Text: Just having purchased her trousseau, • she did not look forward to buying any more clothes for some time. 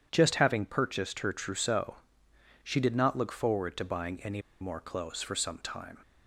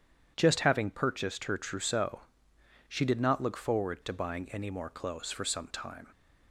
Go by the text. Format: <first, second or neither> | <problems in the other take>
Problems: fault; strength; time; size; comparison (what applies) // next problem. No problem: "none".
second | starts louder than the rest; strong; until 1.1 s; 9 dB // pauses between "any" and "more"; slight; at 4.4 s; 0.19 s long